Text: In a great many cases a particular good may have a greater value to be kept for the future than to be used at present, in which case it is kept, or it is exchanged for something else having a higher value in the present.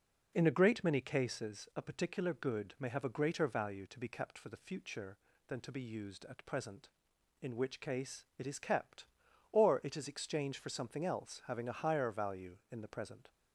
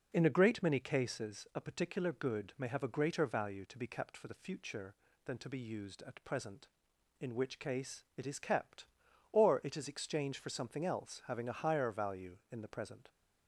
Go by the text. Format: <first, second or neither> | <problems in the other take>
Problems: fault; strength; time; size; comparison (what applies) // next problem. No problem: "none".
neither | none